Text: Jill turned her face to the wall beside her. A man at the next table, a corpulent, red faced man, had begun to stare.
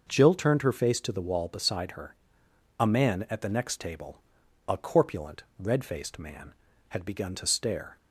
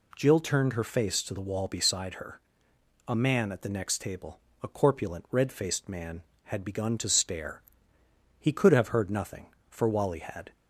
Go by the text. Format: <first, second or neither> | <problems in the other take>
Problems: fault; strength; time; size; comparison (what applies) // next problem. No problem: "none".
first | goes on to say "He could have heard nothing for Wally had"; strong; from 8.3 s on; 2.1 s long